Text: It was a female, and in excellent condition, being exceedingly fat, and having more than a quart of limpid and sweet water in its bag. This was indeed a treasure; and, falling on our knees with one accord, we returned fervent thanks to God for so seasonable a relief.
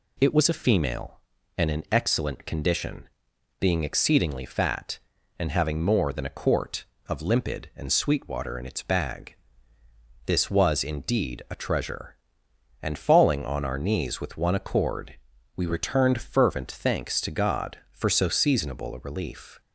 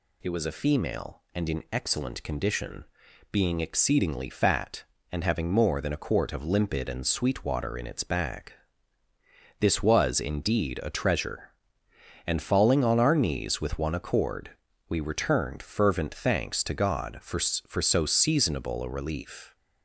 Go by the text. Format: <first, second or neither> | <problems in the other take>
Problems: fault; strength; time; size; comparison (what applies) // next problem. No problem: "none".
first | says "for" twice; at 17.6 s